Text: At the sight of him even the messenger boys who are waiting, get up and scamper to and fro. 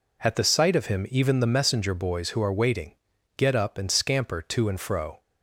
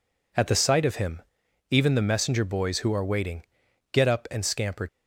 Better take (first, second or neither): first